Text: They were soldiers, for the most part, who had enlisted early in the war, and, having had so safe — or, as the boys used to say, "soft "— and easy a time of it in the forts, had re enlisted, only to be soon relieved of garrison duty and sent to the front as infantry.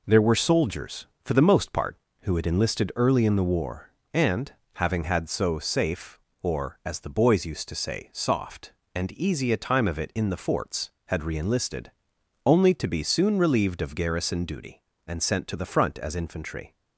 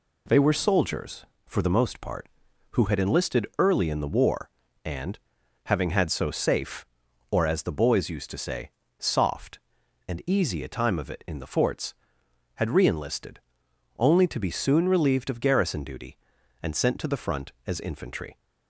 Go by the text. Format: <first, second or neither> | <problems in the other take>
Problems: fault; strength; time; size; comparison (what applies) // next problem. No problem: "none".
second | says "There" for "They"; at 0.0 s